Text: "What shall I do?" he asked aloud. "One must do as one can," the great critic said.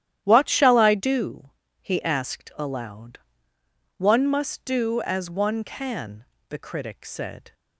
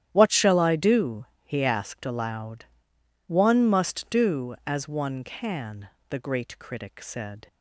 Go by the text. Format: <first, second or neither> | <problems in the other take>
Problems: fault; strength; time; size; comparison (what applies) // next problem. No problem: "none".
second | starts louder than the rest; strong; until 1.2 s; 11.5 dB; strong in the second // skips "great"; at 6.5 s